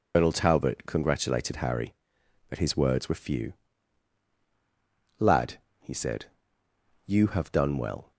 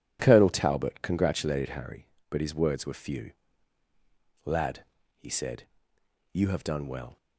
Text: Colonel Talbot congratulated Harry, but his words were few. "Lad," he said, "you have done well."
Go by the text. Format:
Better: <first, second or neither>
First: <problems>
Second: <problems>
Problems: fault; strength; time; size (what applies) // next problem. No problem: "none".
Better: second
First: loses the start of "Colonel"; at 0.1 s; 110 ms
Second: none